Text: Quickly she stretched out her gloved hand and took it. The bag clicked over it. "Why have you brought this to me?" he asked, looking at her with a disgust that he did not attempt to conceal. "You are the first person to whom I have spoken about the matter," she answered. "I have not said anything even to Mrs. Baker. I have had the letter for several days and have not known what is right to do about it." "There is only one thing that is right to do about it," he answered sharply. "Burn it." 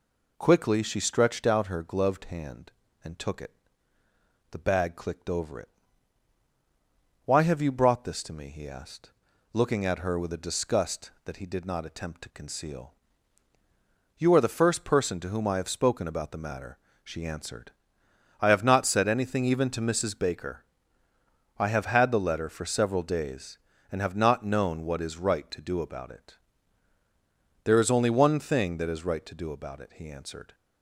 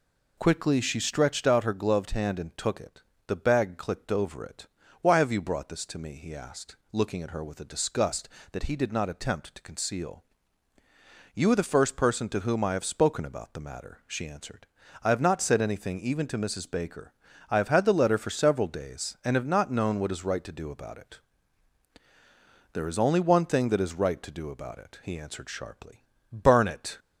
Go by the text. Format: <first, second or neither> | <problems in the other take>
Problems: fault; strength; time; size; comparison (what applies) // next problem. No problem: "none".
second | stops before "sharply Burn it"; at 30.5 s